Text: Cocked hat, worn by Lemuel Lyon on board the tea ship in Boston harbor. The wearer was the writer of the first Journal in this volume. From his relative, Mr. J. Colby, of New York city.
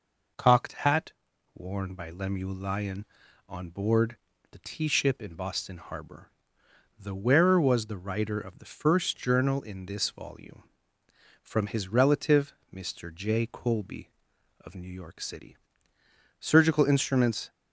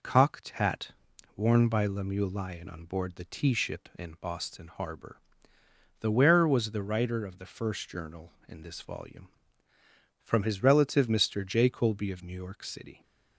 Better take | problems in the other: second | pauses between "board" and "the"; slight; at 4.1 s; 0.34 s long // goes on to say "Surgical instruments"; noticeable; from 16.4 s on; 1.1 s long

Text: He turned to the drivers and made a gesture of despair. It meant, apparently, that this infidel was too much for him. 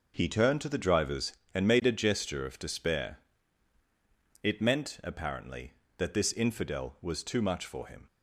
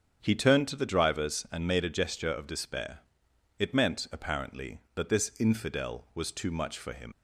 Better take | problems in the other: first | starts louder than the rest; strong; until 1.2 s; 8 dB // leaves "him" unfinished; at 7.1 s; 80 ms

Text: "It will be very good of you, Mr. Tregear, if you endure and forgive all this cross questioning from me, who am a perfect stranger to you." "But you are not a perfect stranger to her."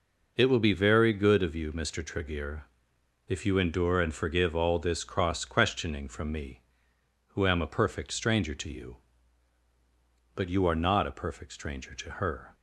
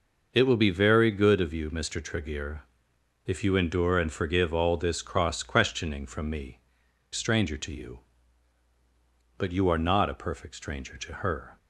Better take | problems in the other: first | skips "who am a perfect"; at 6.8 s

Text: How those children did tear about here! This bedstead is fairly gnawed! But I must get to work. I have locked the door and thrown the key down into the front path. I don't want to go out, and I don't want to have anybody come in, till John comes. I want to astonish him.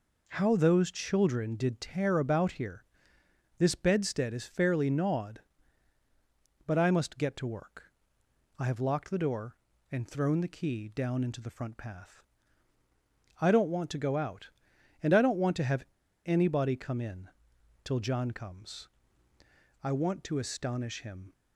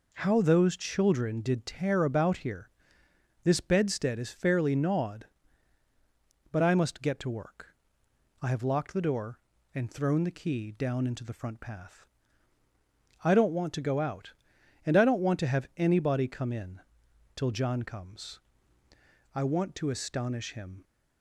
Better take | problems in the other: second | pauses between "have" and "anybody"; at 15.8 s; 0.41 s long

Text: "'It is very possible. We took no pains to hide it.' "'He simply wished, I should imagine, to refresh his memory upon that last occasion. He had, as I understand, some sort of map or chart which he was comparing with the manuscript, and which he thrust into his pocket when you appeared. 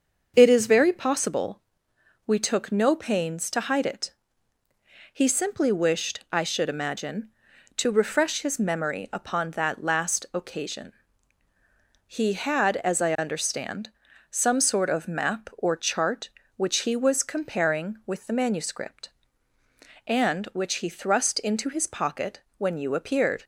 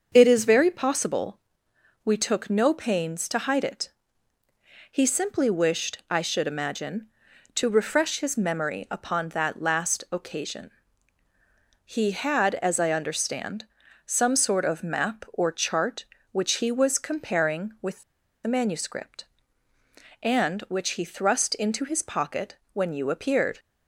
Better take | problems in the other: first | starts louder than the rest; until 1.1 s; 6.5 dB; also in the first // pauses between "with" and "the"; at 18.0 s; 0.42 s long // pauses between "pocket" and "when"; slight; at 22.5 s; 0.16 s long; slight in the first

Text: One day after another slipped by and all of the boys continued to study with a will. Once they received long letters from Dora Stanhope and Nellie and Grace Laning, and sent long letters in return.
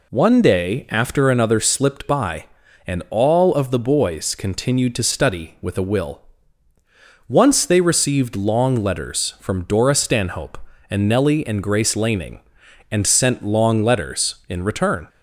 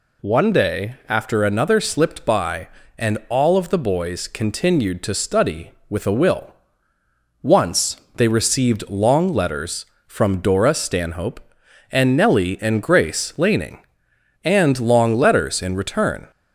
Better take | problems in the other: first | pauses between "Once" and "they"; slight; at 7.9 s; 0.20 s long // skips "sent"; at 14.7 s

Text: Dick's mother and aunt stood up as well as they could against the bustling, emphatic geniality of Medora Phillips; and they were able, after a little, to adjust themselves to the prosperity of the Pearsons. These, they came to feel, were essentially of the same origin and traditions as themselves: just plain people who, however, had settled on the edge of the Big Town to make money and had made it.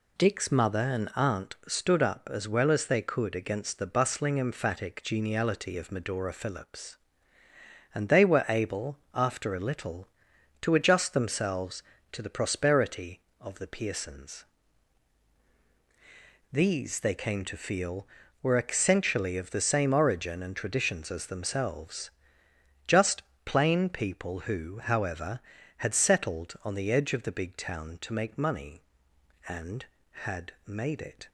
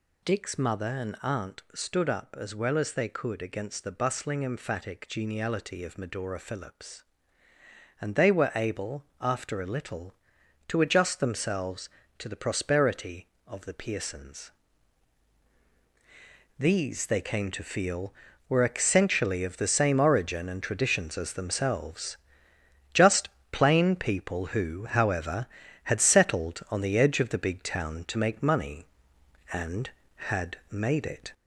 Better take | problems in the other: first | gets louder; noticeable; throughout; 4.5 dB // pauses between "just" and "plain"; slight; at 23.2 s; 0.22 s long; slight in the first

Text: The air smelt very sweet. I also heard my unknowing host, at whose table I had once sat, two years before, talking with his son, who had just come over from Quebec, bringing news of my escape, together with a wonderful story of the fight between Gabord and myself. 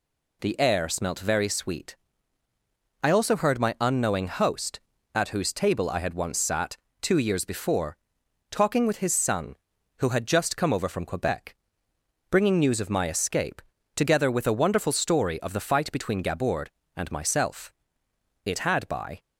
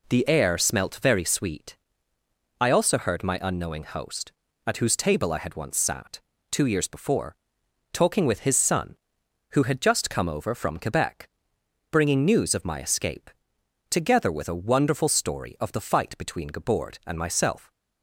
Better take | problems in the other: second | goes on to say "It had by"; noticeable; from 18.4 s on; 0.74 s long

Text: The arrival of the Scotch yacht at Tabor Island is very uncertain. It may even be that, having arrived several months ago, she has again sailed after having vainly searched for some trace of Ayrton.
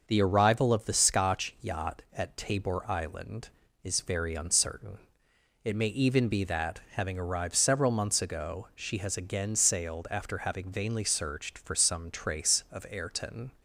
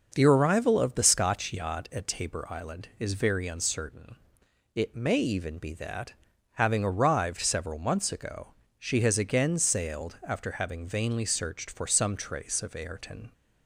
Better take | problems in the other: neither | starts louder than the rest; the same in both

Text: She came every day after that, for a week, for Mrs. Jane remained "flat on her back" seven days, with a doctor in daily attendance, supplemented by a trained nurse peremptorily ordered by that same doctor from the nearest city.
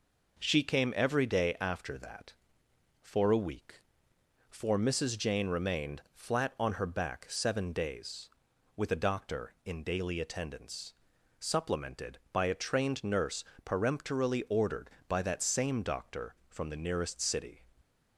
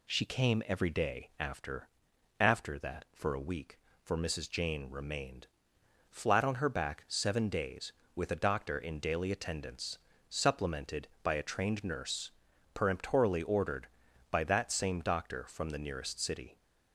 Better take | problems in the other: first | says "after" twice; at 2.4 s // pauses between "remained" and "flat"; noticeable; at 5.4 s; 0.60 s long // pauses between "nurse" and "peremptorily"; at 12.3 s; 0.42 s long; slight in the first

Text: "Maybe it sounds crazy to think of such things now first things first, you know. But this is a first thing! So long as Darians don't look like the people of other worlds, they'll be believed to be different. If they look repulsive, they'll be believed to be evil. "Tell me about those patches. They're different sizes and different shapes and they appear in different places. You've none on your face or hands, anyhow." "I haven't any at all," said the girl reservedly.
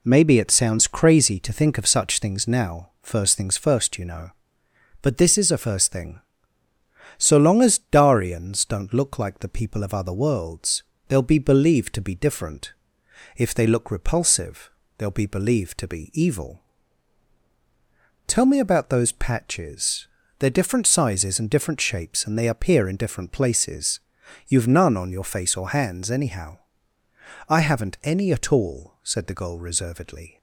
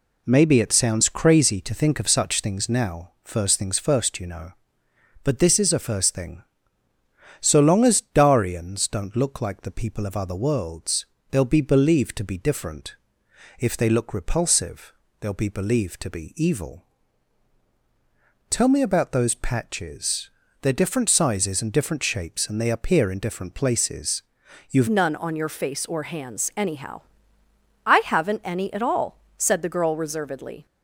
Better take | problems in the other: first | changes voice at "none"; from 24.8 s on; 5.8 s long

